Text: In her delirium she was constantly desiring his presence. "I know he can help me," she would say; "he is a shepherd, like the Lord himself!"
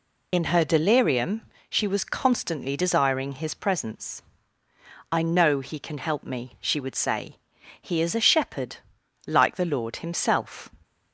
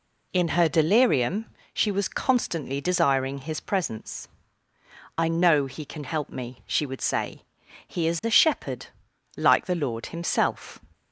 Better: second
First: loses the start of "In"; at 0.3 s; 65 ms // pauses between "delirium" and "she"; slight; at 1.4 s; 0.26 s long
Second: pauses between "delirium" and "she"; slight; at 1.4 s; 0.26 s long

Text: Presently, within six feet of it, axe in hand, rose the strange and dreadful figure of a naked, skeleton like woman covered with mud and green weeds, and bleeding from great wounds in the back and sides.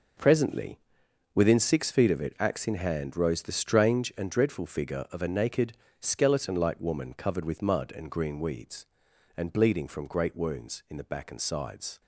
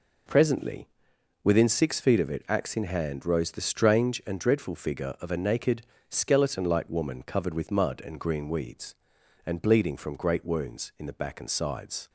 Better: second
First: gets quieter; strong; throughout; 10 dB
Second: none

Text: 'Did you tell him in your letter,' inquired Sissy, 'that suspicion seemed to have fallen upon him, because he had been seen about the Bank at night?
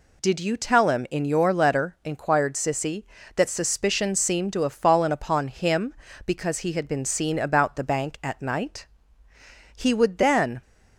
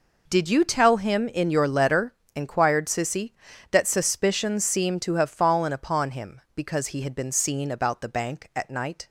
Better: second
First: goes on to say "He would then"; noticeable; from 9.7 s on; 0.86 s long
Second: none

